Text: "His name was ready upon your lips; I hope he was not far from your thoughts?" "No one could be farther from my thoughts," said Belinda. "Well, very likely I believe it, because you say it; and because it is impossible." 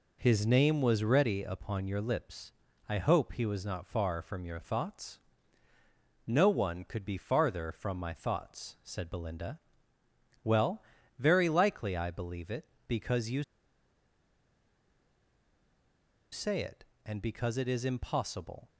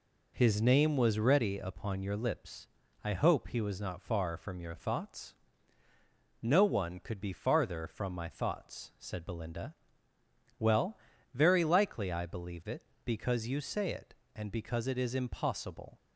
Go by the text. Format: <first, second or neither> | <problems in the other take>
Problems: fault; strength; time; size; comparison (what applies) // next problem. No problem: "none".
second | pauses between "you" and "say"; strong; at 13.4 s; 2.8 s long